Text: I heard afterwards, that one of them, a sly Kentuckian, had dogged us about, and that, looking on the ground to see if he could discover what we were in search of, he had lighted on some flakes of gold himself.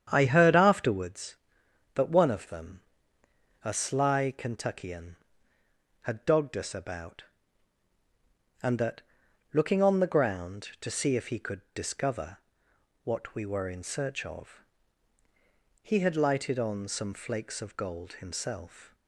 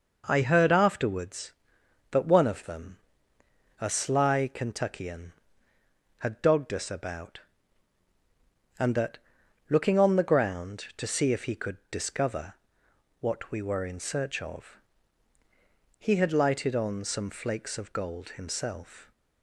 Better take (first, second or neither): second